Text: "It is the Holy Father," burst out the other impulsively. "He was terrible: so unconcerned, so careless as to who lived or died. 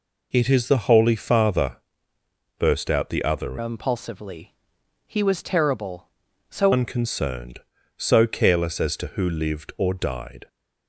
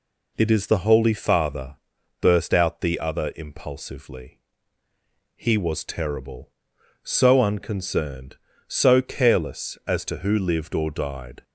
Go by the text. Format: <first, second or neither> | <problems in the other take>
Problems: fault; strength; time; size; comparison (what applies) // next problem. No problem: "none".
second | changes voice from "impulsively" to "so"; from 3.5 to 6.7 s; 3.2 s long